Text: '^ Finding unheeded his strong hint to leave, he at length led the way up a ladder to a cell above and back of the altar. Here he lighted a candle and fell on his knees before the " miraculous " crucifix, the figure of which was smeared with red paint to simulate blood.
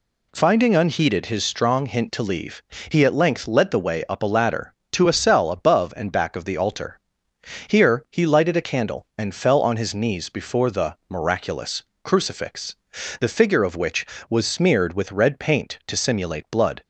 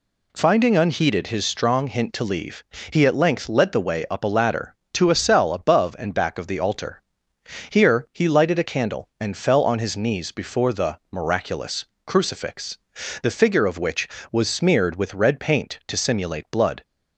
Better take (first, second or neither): neither